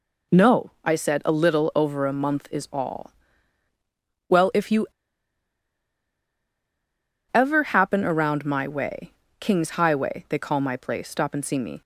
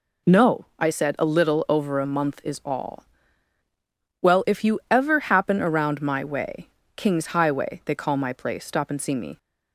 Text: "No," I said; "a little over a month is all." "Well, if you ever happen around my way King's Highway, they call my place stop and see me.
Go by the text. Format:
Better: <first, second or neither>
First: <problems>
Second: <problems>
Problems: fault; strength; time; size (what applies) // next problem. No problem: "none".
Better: second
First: pauses between "you" and "ever"; strong; at 4.8 s; 2.4 s long // pauses between "way" and "King's"; slight; at 9.1 s; 0.26 s long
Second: pauses between "way" and "King's"; slight; at 6.6 s; 0.26 s long